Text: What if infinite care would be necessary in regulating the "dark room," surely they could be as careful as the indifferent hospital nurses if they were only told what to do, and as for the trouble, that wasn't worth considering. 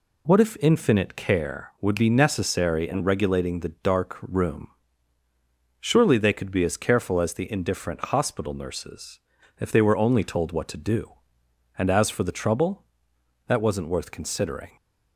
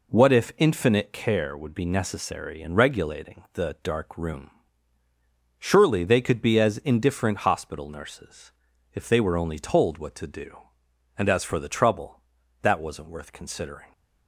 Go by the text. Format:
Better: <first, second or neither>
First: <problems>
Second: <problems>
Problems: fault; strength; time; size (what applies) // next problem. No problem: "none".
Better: first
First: pauses between "nurses" and "if"; at 9.1 s; 0.40 s long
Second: skips "careful as the"; at 6.7 s // pauses between "nurses" and "if"; at 8.4 s; 0.42 s long